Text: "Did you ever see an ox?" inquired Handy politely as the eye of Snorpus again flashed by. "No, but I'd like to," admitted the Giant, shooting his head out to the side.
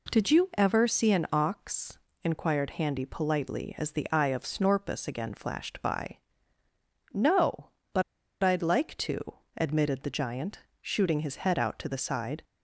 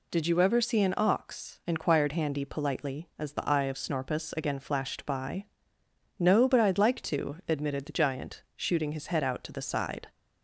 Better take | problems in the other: second | pauses between "but" and "I'd"; at 8.0 s; 0.40 s long

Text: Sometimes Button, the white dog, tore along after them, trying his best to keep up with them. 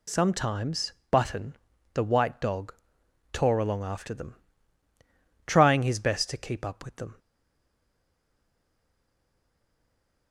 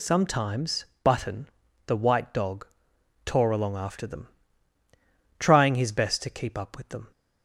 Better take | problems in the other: second | pauses between "Sometimes" and "Button"; slight; at 0.9 s; 0.18 s long; slight in the second // stays silent after the last word; strong; from 7.1 s on; 3.2 s long

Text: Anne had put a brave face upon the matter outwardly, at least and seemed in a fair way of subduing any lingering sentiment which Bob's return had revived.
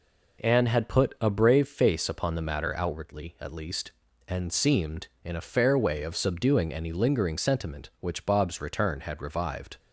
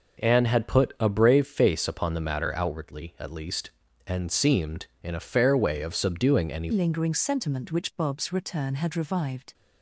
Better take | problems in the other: first | changes voice at "lingering"; from 6.7 s on; 2.8 s long

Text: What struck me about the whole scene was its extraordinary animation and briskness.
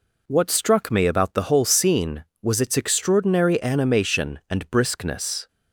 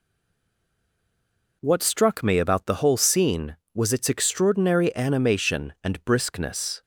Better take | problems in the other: first | stays silent before the first word; noticeable; until 1.6 s; 1.6 s long

